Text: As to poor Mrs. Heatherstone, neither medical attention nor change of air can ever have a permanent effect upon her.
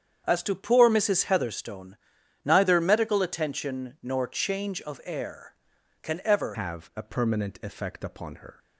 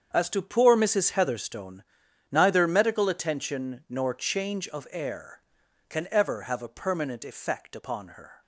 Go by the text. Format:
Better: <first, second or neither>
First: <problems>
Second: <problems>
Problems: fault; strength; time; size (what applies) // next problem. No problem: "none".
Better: second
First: starts louder than the rest; strong; until 1.2 s; 8 dB // changes voice at "have"; from 6.5 s on; 2.0 s long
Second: starts louder than the rest; strong; until 1.1 s; 7.5 dB